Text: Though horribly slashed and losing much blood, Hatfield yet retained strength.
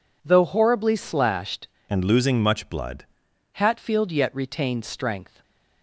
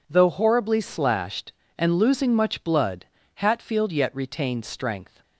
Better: second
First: changes voice from "and" to "blood"; from 1.8 to 3.0 s; 1.2 s long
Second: none

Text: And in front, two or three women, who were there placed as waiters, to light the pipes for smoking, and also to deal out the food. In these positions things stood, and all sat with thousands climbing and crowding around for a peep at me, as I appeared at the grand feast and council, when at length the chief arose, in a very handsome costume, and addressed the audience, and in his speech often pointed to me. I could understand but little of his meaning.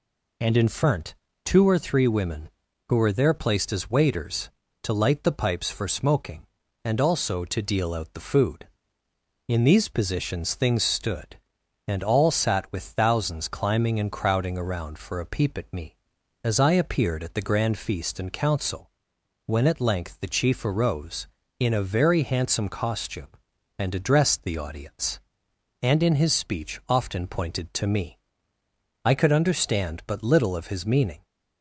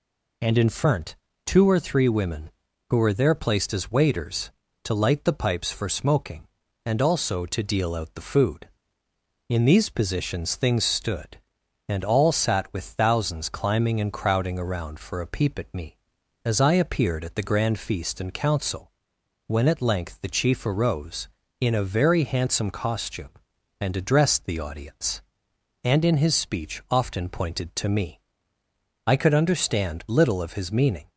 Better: first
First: none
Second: skips "but"; at 30.0 s

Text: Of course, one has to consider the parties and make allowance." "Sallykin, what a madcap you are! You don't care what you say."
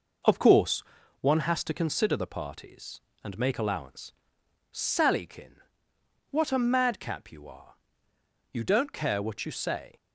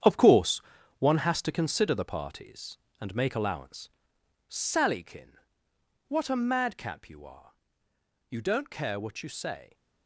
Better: first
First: none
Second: gets quieter; strong; throughout; 10 dB

